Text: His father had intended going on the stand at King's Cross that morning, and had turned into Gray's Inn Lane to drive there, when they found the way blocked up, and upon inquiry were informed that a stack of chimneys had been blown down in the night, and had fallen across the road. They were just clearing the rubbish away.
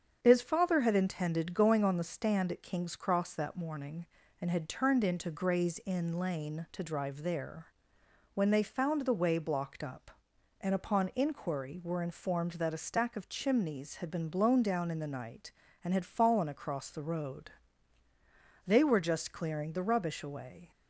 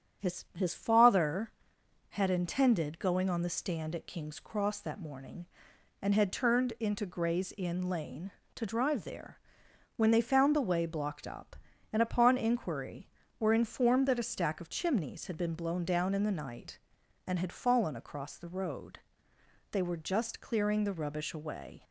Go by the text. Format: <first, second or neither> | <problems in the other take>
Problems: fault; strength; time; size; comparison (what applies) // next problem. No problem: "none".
first | starts louder than the rest; strong; until 1.3 s; 8.5 dB; strong in the first // says "His" twice; at 0.5 s